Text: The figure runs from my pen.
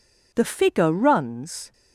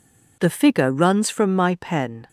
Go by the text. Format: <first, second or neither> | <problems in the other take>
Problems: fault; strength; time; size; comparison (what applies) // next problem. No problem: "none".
second | stops before "from my pen"; at 1.7 s